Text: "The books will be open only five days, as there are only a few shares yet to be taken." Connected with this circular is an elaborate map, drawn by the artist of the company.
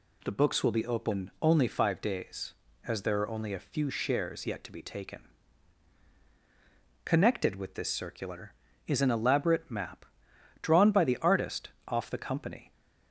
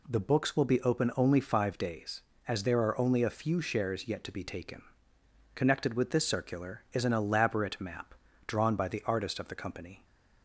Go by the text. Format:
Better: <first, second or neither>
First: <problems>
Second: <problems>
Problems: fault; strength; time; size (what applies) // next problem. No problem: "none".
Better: second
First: says "off" for "of"; at 11.8 s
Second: none